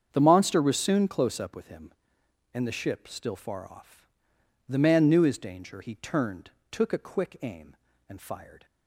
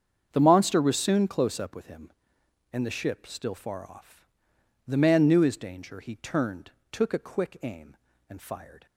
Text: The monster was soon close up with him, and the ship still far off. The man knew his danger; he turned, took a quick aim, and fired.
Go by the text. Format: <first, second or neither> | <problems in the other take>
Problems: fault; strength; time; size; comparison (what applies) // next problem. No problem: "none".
neither | starts louder than the rest; strong; the same in both